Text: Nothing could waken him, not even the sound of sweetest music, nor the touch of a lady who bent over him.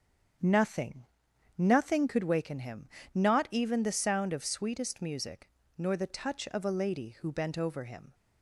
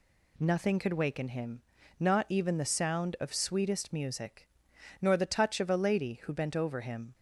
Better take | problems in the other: second | starts louder than the rest; strong; until 1.9 s; 8 dB // says "Nothing" twice; at 1.5 s

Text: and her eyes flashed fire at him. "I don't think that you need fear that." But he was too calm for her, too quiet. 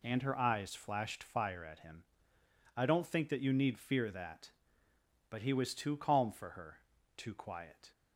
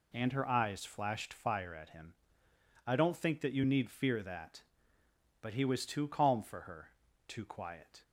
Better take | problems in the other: neither | none

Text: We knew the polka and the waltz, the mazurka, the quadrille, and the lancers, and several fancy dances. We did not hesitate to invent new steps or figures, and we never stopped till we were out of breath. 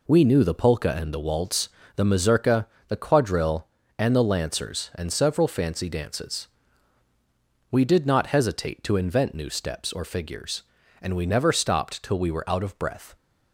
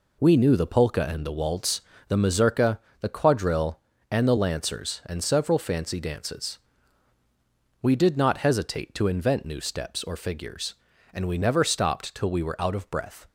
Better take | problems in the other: neither | none

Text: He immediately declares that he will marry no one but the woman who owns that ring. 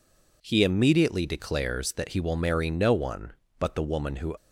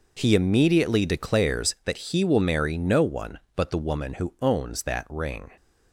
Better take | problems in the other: second | stops before "owns that ring"; at 4.3 s

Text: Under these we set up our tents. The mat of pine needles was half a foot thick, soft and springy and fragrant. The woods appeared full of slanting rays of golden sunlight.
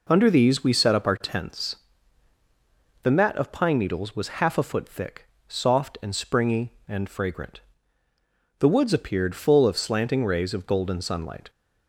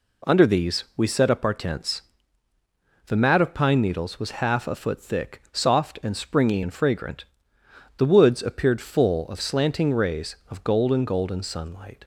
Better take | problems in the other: first | says "golden" twice; at 11.0 s

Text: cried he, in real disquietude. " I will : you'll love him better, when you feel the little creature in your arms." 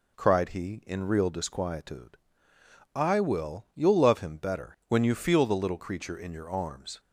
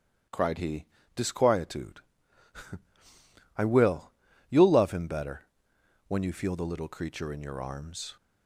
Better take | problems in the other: first | skips "in real"; at 1.0 s

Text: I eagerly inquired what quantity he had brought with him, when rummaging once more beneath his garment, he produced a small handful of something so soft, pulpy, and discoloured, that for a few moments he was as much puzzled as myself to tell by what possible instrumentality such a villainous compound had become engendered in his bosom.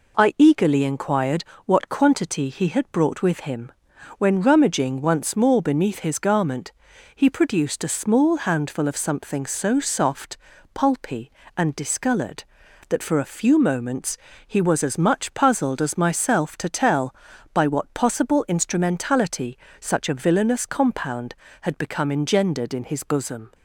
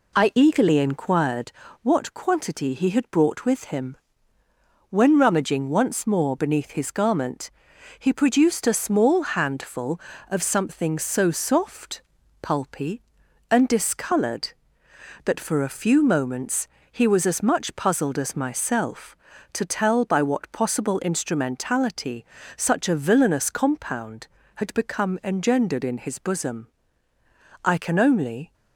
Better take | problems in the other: first | pauses between "inquired" and "what"; slight; at 1.5 s; 0.30 s long; slight in the first // pauses between "moments" and "he"; slight; at 16.6 s; 0.24 s long; slight in the first // pauses between "instrumentality" and "such"; slight; at 22.2 s; 0.32 s long; slight in the first // goes on to say "I can only"; noticeable; from 27.6 s on; 0.88 s long

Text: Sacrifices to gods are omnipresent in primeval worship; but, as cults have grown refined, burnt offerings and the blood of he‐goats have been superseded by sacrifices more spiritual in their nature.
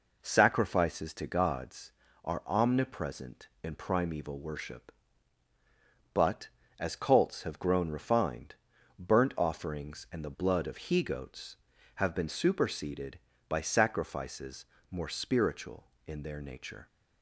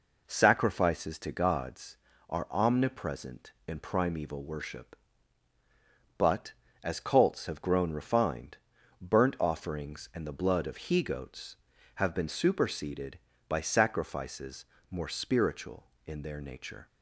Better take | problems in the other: neither | pauses between "sacrifices" and "more"; slight; the same in both

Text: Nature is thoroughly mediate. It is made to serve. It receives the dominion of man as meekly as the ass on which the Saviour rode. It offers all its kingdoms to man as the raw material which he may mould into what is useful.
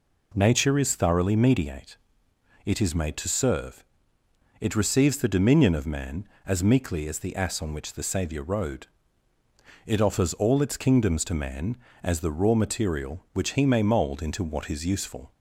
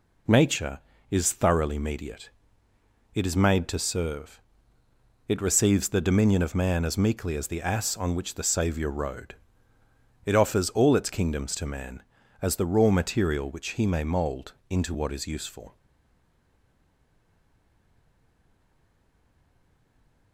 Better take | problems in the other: first | pauses between "mould" and "into"; slight; at 14.5 s; 0.18 s long // stays silent after the last word; strong; from 15.7 s on; 4.6 s long

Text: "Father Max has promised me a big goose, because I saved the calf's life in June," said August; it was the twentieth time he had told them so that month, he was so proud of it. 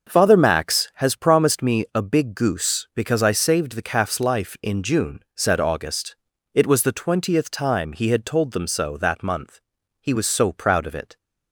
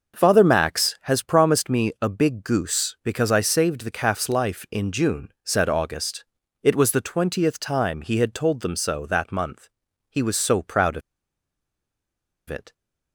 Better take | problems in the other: first | starts louder than the rest; until 1.2 s; 6 dB; also in the first // pauses between "of" and "it"; strong; at 11.0 s; 1.4 s long

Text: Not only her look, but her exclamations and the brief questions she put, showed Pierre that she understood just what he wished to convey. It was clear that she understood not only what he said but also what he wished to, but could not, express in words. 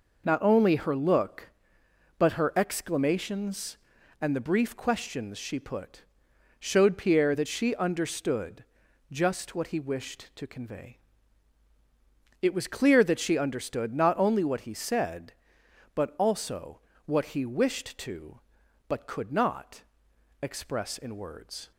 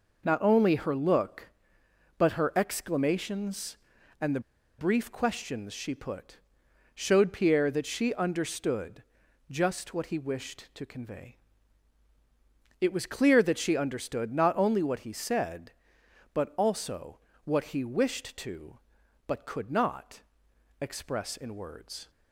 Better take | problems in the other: first | pauses between "the" and "brief"; at 4.4 s; 0.38 s long // pauses between "understood" and "just"; noticeable; at 9.0 s; 0.48 s long; noticeable in the first // pauses between "also" and "what"; slight; at 17.1 s; 0.26 s long; slight in the first

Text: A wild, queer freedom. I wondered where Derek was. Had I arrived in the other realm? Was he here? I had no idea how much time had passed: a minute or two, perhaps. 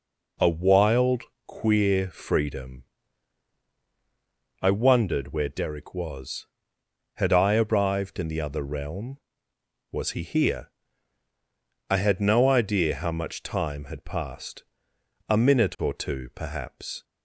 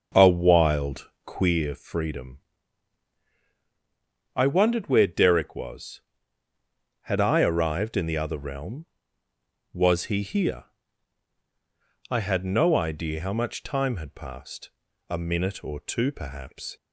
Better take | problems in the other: first | starts louder than the rest; until 1.5 s; 6.5 dB

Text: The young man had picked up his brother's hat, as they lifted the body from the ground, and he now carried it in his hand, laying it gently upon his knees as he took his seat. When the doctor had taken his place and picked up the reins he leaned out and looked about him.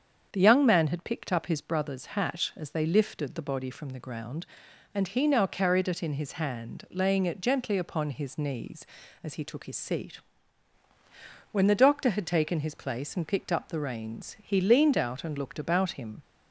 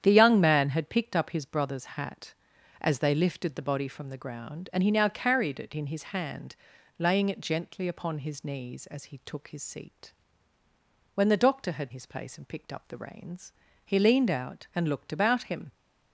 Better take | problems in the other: first | starts louder than the rest; strong; until 1.0 s; 9 dB; strong in the first // skips "taken"; at 11.9 s // pauses between "reins" and "he"; slight; at 13.5 s; 0.34 s long

